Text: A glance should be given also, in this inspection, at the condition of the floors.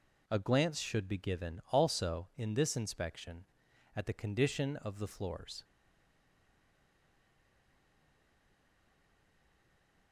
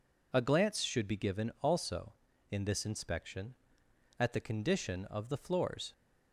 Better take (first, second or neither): second